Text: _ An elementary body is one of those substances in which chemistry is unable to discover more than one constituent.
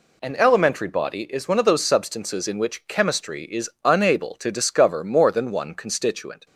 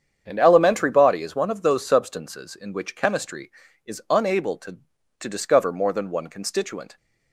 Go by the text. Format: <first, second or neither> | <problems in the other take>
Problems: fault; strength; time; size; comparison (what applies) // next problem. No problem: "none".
first | starts louder than the rest; strong; until 1.2 s; 8 dB // says "to" twice; at 5.1 s